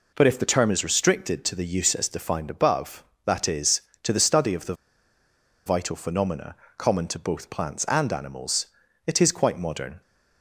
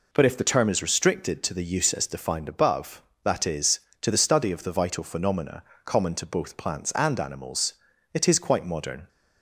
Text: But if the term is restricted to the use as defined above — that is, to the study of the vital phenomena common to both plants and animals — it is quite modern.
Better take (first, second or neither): second